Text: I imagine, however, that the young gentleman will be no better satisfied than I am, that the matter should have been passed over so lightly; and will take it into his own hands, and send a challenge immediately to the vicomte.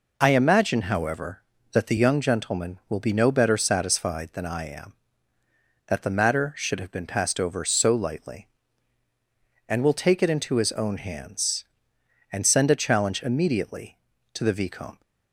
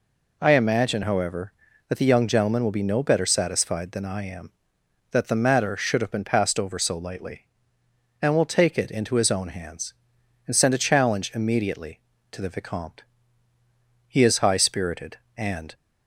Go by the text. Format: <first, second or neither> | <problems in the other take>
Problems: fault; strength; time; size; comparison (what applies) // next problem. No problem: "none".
first | goes on to say "He is high spirited and"; strong; from 14.0 s on; 1.6 s long